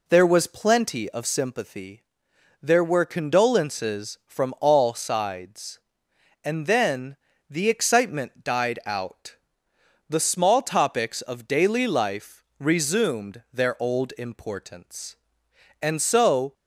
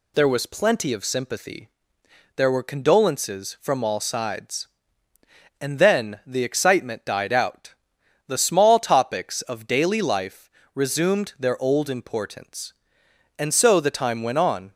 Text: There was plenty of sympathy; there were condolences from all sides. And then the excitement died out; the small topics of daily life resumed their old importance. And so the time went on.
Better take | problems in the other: second | pauses between "then" and "the"; slight; at 7.1 s; 0.32 s long // pauses between "life" and "resumed"; slight; at 12.4 s; 0.16 s long; slight in the second // stops before "the time went on"; at 16.5 s

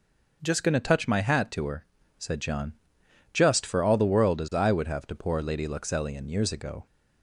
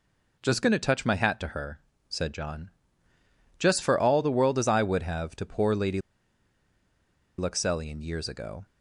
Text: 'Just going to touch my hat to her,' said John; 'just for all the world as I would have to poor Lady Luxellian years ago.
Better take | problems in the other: first | pauses between "Lady" and "Luxellian"; strong; at 5.9 s; 1.3 s long

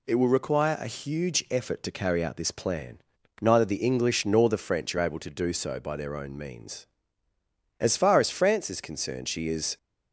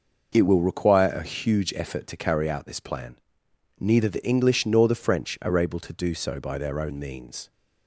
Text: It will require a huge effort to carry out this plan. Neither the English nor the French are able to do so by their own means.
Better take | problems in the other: second | goes on to say "As far as France is concerned she is"; strong; from 7.7 s on; 1.9 s long

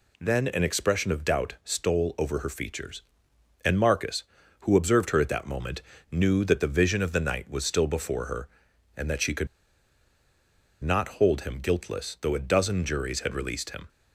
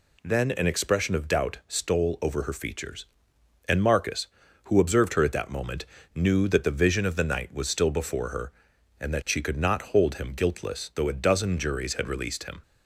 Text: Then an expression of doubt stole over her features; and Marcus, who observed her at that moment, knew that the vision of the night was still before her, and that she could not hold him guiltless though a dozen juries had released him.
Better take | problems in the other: second | pauses between "could" and "not"; strong; at 9.4 s; 1.3 s long

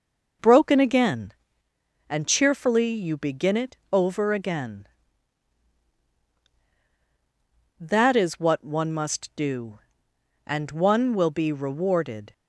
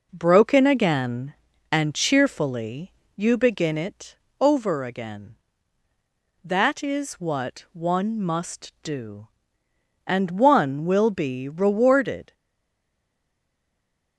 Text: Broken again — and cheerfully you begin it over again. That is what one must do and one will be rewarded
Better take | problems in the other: first | pauses between "cheerfully" and "you"; slight; at 2.9 s; 0.22 s long // pauses between "it" and "over"; slight; at 4.1 s; 0.26 s long; slight in the first // stays silent after the last word; noticeable; from 12.3 s on; 1.8 s long

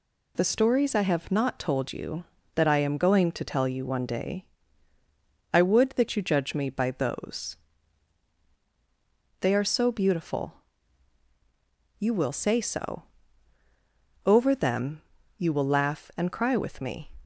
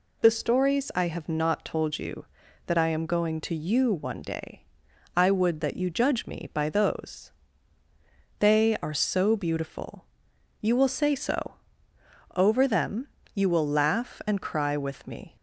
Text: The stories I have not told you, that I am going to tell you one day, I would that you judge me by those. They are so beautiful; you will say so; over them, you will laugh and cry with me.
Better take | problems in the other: first | skips "tell"; at 3.5 s

